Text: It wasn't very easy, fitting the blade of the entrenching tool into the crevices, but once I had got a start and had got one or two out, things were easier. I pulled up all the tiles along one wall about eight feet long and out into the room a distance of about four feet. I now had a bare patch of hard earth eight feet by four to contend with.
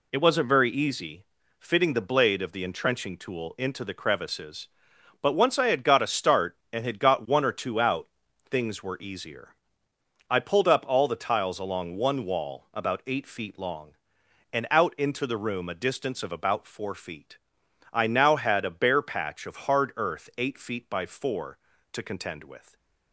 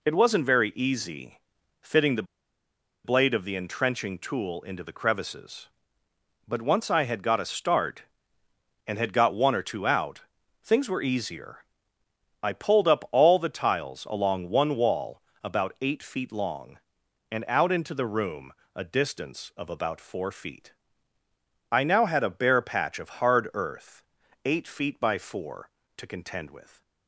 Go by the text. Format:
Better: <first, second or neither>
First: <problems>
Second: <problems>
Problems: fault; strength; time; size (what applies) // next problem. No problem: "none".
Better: first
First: none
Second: pauses between "the" and "blade"; noticeable; at 2.2 s; 0.81 s long // pauses between "wall" and "about"; slight; at 15.1 s; 0.24 s long // pauses between "room" and "a"; slight; at 18.5 s; 0.20 s long // pauses between "earth" and "eight"; at 24.0 s; 0.44 s long